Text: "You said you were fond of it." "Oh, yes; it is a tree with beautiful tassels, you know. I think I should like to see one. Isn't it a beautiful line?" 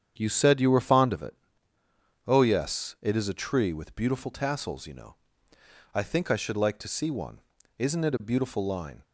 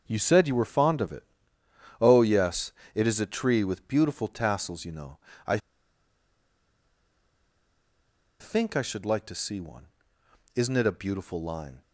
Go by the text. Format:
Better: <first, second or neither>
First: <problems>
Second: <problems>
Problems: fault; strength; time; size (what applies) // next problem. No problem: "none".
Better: first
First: starts louder than the rest; strong; until 1.1 s; 8.5 dB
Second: starts louder than the rest; until 1.0 s; 7 dB // pauses between "I" and "think"; strong; at 5.5 s; 2.8 s long